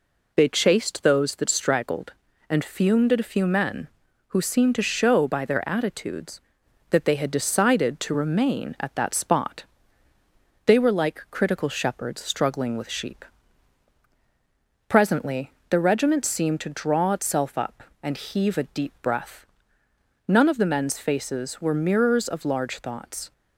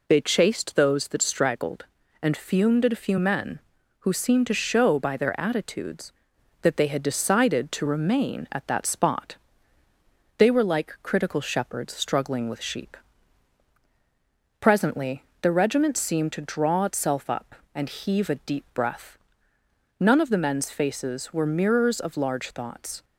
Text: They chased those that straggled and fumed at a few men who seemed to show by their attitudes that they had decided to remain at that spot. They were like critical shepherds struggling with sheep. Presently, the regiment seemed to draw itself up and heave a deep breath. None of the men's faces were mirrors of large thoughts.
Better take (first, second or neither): neither